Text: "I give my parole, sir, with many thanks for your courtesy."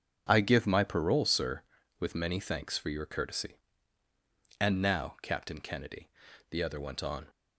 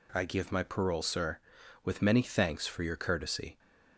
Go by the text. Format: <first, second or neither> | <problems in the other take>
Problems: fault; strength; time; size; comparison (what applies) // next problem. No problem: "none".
second | starts louder than the rest; strong; until 1.2 s; 7.5 dB // goes on to say "And now Captain Kennedy the other went on"; strong; from 4.5 s on; 2.6 s long